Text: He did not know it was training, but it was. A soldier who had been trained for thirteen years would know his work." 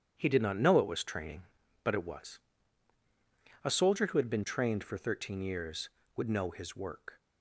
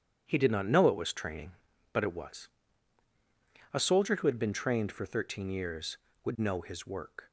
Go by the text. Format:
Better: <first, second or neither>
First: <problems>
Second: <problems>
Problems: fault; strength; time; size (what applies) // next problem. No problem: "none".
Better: neither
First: starts louder than the rest; strong; until 1.1 s; 9 dB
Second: starts louder than the rest; strong; until 1.2 s; 9.5 dB